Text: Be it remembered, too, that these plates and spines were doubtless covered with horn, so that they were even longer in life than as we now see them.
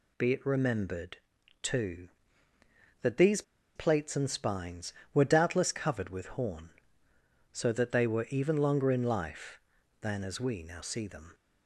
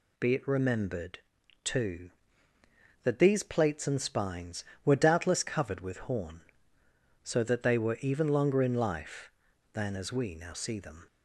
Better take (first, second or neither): second